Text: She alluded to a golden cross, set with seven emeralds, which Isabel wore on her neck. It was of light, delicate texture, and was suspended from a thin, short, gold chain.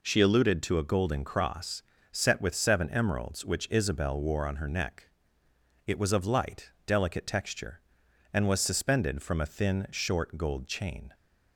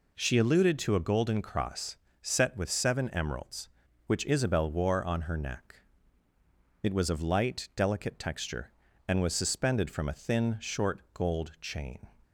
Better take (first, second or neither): neither